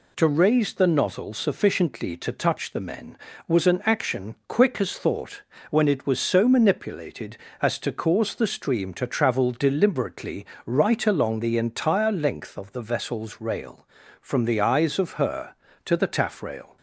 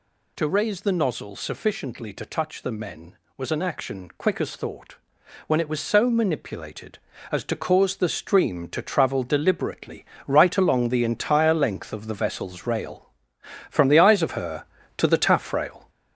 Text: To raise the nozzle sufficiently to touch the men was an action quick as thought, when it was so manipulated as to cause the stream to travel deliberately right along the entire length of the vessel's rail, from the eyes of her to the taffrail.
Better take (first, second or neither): first